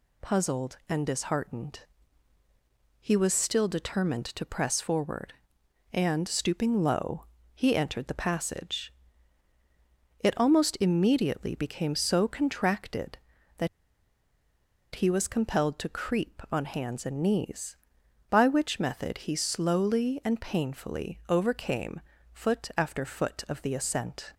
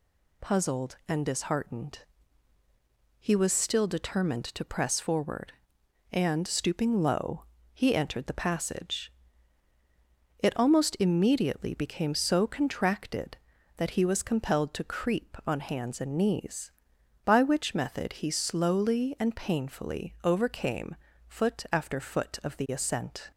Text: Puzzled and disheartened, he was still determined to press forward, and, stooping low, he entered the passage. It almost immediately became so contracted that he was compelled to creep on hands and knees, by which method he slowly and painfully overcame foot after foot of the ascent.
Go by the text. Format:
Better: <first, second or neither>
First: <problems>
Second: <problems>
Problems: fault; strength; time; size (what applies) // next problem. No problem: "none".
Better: second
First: pauses between "that" and "he"; strong; at 13.6 s; 1.2 s long // pauses between "overcame" and "foot"; slight; at 22.0 s; 0.32 s long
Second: pauses between "overcame" and "foot"; slight; at 20.9 s; 0.32 s long